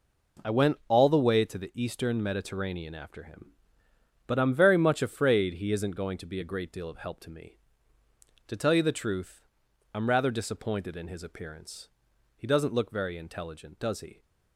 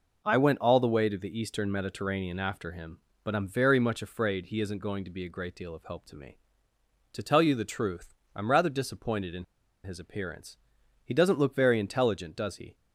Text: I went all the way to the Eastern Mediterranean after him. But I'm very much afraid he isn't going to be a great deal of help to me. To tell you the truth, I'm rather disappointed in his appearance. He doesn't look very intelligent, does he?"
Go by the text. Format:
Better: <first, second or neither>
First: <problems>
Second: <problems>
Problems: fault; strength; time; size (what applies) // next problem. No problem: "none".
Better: first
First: none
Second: pauses between "in" and "his"; at 9.4 s; 0.39 s long